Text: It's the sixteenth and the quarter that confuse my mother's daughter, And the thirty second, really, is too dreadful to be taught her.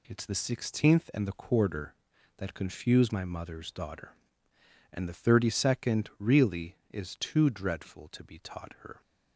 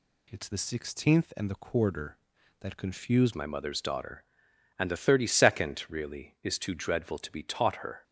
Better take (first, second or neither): first